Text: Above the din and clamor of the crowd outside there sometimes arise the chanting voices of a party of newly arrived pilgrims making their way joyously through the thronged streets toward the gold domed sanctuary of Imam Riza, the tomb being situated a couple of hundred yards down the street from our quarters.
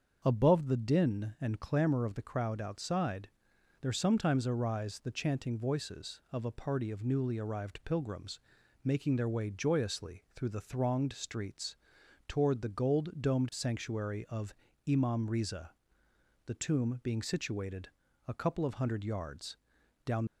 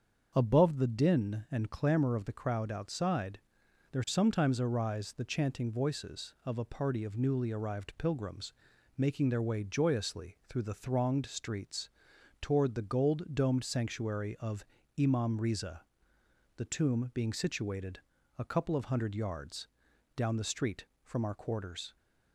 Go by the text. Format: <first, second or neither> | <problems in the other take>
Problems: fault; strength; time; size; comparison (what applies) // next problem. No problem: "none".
second | starts louder than the rest; until 1.2 s; 7 dB; also in the second // pauses between "outside" and "there"; noticeable; at 3.2 s; 0.52 s long; noticeable in the second // pauses between "pilgrims" and "making"; noticeable; at 8.3 s; 0.46 s long; noticeable in the second // pauses between "streets" and "toward"; noticeable; at 11.7 s; 0.54 s long; noticeable in the second // pauses between "of" and "Imam"; slight; at 14.5 s; 0.34 s long; slight in the second // pauses between "situated" and "a"; at 17.8 s; 0.38 s long; also in the second // pauses between "yards" and "down"; noticeable; at 19.5 s; 0.50 s long; noticeable in the second // stops before "the street from our quarters"; at 20.2 s